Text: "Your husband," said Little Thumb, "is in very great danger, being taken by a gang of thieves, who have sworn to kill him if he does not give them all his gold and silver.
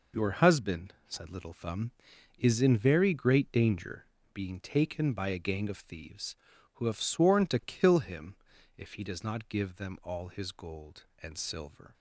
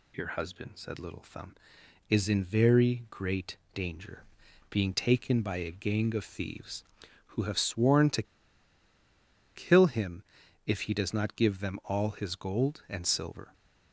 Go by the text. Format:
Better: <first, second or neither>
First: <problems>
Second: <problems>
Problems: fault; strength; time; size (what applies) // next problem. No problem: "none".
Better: first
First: pauses between "him" and "if"; at 8.3 s; 0.42 s long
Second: pauses between "great" and "danger"; slight; at 3.5 s; 0.16 s long // pauses between "to" and "kill"; strong; at 8.2 s; 1.3 s long // pauses between "him" and "if"; at 10.2 s; 0.42 s long